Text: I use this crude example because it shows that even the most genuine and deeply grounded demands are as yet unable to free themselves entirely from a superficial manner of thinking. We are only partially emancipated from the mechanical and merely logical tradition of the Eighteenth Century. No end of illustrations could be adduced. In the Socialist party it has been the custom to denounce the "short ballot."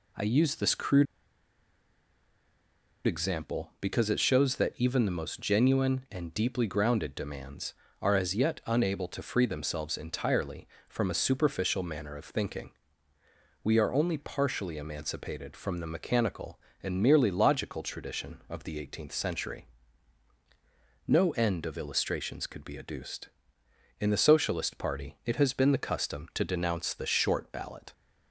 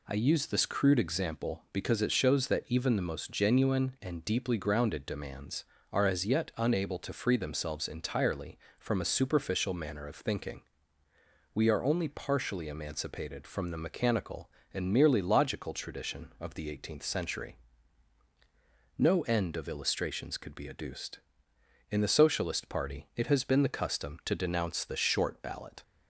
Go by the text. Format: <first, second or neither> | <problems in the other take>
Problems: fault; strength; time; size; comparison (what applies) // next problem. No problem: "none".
second | pauses between "crude" and "example"; strong; at 1.0 s; 2.0 s long